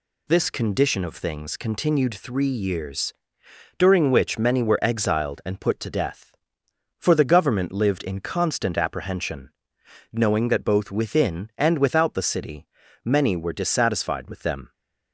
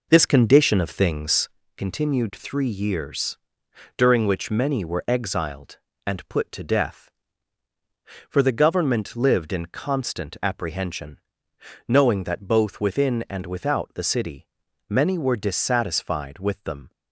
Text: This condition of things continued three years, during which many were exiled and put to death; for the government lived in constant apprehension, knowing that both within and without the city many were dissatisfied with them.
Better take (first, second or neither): first